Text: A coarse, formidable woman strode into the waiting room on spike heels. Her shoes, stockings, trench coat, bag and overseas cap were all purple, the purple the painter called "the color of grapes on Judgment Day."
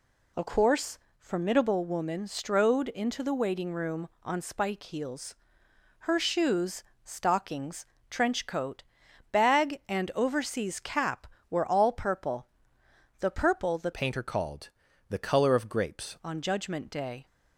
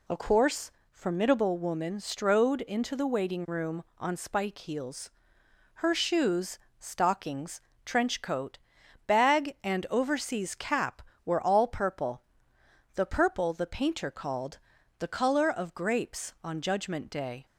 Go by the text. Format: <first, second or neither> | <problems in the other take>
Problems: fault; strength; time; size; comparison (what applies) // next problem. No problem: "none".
second | changes voice from "painter" to "grapes"; from 13.9 to 16.1 s; 2.2 s long // pauses between "called" and "the"; at 14.6 s; 0.40 s long; also in the second